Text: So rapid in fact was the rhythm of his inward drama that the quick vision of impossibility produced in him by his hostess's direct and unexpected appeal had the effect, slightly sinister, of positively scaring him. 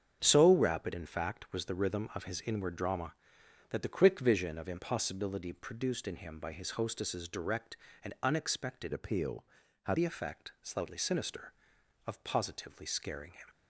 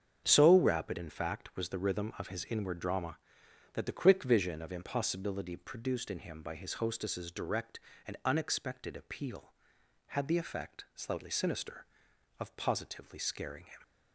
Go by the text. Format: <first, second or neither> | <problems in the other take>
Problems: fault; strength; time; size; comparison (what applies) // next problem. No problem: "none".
second | starts louder than the rest; strong; until 1.2 s; 7.5 dB; strong in the second // changes voice from "appeal" to "had"; from 8.9 to 9.9 s; 1.0 s long